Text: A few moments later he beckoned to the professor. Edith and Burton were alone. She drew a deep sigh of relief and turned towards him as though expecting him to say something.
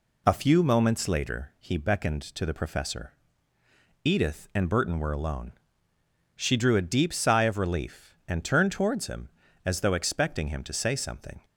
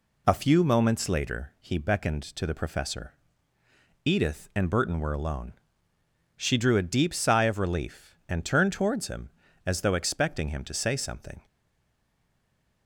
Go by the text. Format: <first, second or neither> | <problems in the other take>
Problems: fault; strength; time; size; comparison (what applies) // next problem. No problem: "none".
first | stays silent after the last word; noticeable; from 11.4 s on; 1.4 s long